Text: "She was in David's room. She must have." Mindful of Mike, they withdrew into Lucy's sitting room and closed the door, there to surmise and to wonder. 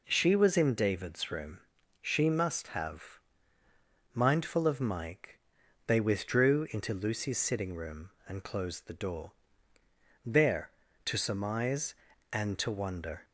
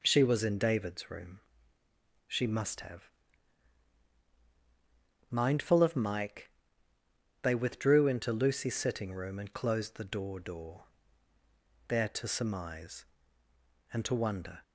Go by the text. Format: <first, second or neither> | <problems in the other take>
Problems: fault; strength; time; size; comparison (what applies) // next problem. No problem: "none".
first | says "door" twice; at 10.4 s